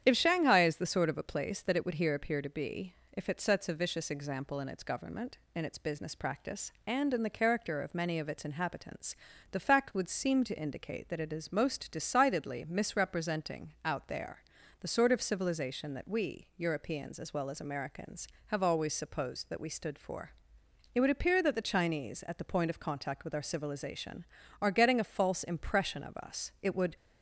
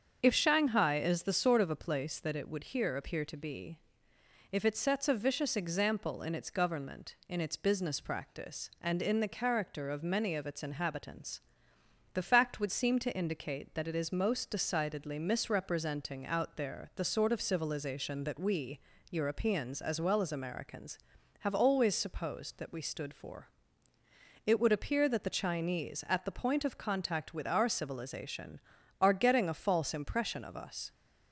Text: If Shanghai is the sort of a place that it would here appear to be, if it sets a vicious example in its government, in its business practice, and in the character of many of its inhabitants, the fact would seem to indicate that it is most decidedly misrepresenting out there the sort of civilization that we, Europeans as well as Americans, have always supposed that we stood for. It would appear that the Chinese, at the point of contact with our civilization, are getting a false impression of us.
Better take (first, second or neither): second